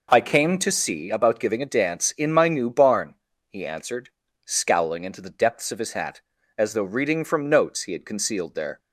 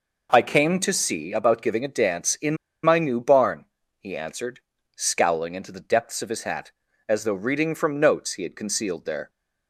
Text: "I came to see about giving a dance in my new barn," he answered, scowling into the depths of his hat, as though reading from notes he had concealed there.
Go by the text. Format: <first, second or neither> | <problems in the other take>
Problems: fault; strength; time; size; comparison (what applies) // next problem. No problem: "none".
first | pauses between "in" and "my"; slight; at 2.5 s; 0.28 s long